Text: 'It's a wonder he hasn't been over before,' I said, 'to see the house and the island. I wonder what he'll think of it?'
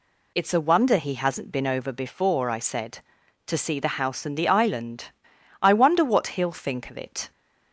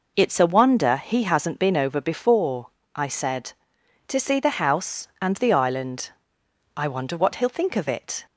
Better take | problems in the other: neither | none

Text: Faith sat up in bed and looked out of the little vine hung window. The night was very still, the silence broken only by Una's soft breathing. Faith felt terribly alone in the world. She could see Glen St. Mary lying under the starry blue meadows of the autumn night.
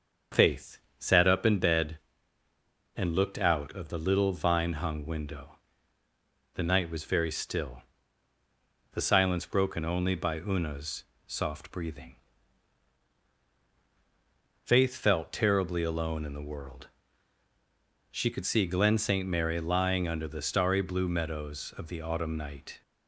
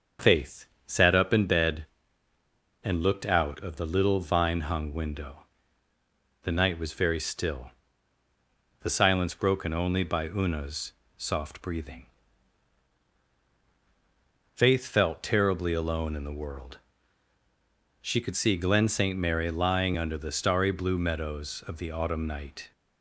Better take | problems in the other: neither | starts louder than the rest; the same in both // pauses between "Faith" and "sat"; slight; the same in both // pauses between "Una's" and "soft"; slight; the same in both

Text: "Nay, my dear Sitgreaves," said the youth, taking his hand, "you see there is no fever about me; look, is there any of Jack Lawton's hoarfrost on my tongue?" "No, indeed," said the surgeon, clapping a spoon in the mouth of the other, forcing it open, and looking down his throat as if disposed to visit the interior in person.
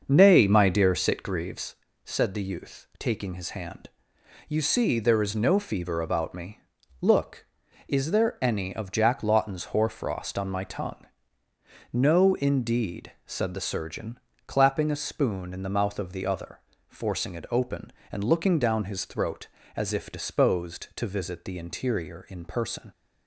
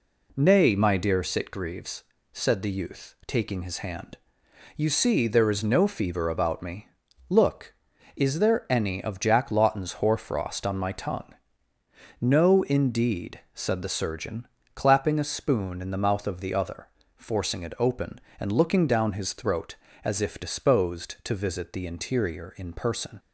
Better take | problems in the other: second | starts louder than the rest; until 1.8 s; 6.5 dB

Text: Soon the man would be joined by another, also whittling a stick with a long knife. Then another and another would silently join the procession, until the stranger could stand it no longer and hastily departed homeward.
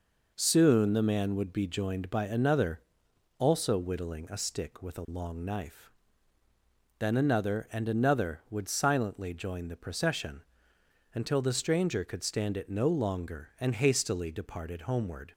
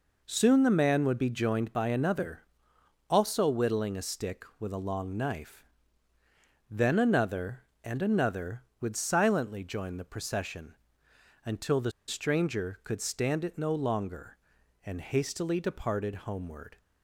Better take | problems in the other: first | pauses between "the" and "stranger"; slight; at 11.9 s; 0.16 s long

